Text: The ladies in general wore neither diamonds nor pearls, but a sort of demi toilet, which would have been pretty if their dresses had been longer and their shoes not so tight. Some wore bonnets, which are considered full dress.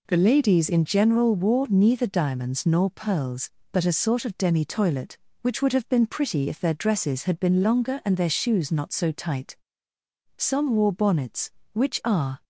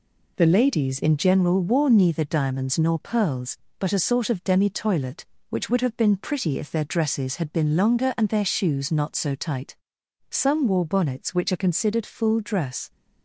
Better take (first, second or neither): second